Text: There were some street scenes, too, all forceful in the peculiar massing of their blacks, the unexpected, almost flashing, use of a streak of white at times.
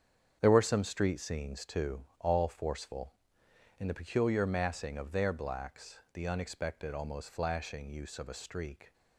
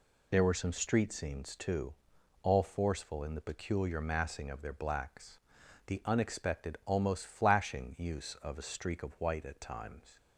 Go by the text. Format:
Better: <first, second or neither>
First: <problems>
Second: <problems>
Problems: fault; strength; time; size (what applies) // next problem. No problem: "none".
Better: second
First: starts louder than the rest; strong; until 1.4 s; 7.5 dB // stops before "of white at times"; at 8.9 s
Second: none